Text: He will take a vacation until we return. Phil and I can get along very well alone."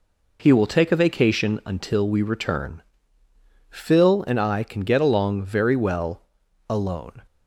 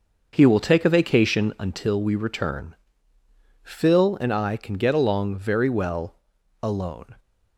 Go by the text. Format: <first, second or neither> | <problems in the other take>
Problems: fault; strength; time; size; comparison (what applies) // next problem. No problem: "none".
first | starts louder than the rest; noticeable; until 1.9 s; 6 dB // pauses between "well" and "alone"; at 6.1 s; 0.44 s long; also in the first